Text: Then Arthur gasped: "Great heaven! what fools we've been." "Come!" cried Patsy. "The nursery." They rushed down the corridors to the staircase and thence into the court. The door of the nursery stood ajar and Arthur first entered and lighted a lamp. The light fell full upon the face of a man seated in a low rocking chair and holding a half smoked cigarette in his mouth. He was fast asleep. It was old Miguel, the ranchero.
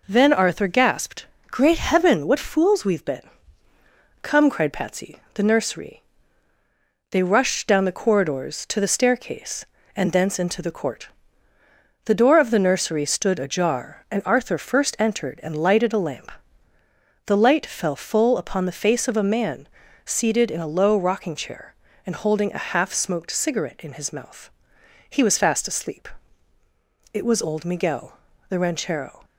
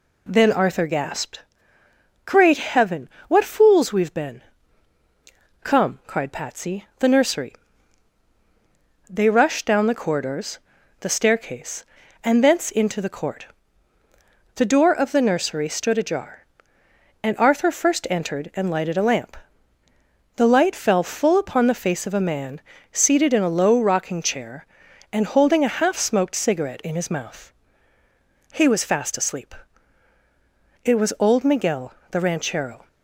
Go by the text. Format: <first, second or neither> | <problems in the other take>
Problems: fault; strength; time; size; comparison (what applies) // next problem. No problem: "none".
first | skips "to"; at 10.7 s // pauses between "man" and "seated"; slight; at 22.5 s; 0.32 s long; also in the first